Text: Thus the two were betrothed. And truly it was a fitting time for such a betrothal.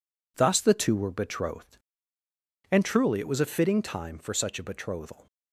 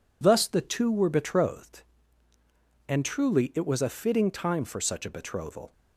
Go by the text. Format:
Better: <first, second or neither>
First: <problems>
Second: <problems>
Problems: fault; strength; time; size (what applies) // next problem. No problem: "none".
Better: neither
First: none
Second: none